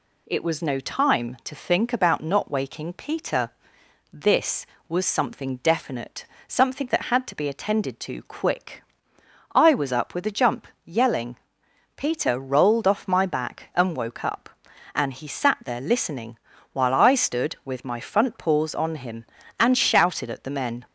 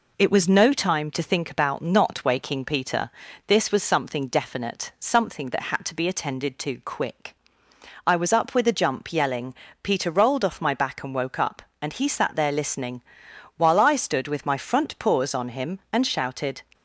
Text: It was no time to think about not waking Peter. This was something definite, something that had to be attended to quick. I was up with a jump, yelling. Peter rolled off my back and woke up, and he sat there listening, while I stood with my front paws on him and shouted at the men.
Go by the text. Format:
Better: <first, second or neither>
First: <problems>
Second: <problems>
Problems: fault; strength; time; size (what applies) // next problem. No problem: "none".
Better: first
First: none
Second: stops before "at the men"; at 16.7 s